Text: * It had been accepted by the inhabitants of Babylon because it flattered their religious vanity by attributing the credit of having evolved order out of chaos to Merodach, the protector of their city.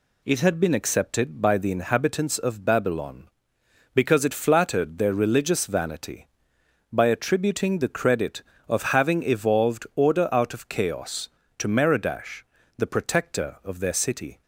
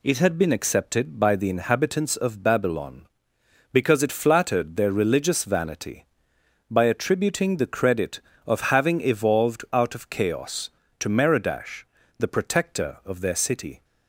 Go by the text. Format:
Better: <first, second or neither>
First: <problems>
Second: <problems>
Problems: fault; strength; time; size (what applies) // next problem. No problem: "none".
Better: first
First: none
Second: skips "order"; at 9.6 s